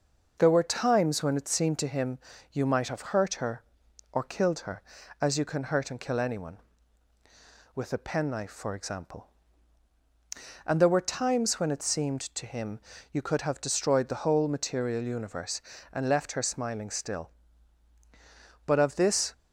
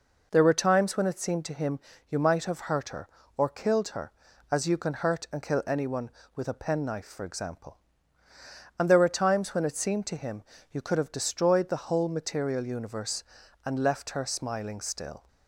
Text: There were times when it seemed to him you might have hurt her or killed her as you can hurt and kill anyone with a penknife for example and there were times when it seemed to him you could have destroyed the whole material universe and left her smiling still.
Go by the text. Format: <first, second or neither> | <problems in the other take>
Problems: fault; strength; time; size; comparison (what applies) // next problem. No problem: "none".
second | pauses between "him" and "you"; slight; at 2.1 s; 0.34 s long; slight in the second // pauses between "him" and "you"; slight; at 12.7 s; 0.32 s long; slight in the second // goes on to say "But of this"; noticeable; from 18.6 s on; 0.66 s long